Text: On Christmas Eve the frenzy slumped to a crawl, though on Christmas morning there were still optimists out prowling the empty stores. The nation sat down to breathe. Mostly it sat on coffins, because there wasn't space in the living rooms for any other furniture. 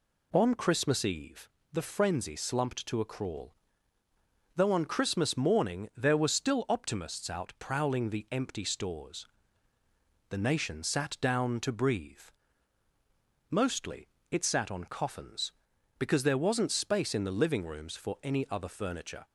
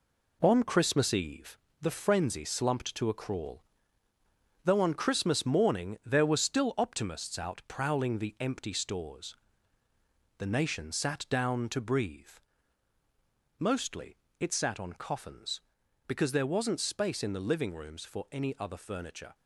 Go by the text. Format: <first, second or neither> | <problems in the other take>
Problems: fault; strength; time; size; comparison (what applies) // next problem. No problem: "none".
first | gets quieter; throughout; 6.5 dB // pauses between "Eve" and "the"; slight; at 1.5 s; 0.24 s long; slight in the first // pauses between "Mostly" and "it"; slight; at 14.1 s; 0.22 s long; slight in the first